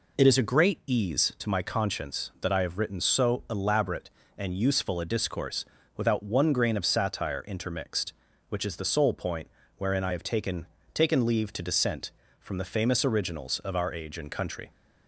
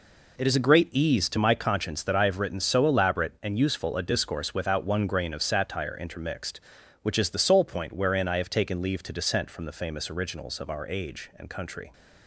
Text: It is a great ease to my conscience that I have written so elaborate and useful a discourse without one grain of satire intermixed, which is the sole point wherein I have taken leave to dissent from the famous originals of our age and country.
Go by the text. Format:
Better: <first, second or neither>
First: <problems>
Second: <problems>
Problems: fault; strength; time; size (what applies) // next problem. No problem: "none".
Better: second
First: pauses between "discourse" and "without"; slight; at 5.6 s; 0.32 s long // pauses between "point" and "wherein"; slight; at 9.4 s; 0.26 s long // says "taken" twice; at 10.9 s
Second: none